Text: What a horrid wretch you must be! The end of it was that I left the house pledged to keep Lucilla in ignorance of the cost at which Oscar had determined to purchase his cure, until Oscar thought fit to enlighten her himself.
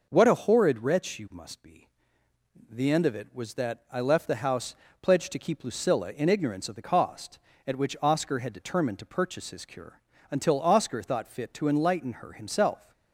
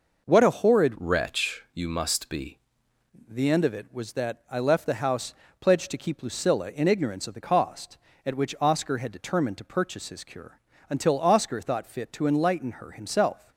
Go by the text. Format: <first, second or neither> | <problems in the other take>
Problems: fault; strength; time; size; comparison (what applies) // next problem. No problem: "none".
first | changes voice from "wretch" to "be"; from 0.9 to 2.5 s; 1.6 s long // pauses between "house" and "pledged"; slight; at 5.3 s; 0.28 s long; slight in the first